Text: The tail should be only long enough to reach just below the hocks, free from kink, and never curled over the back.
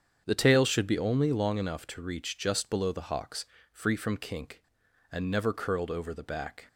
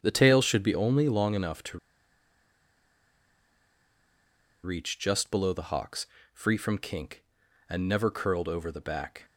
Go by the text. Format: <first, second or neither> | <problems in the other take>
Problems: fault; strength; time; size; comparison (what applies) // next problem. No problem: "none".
first | starts louder than the rest; strong; until 1.0 s; 8 dB; strong in the first // pauses between "to" and "reach"; strong; at 1.7 s; 2.8 s long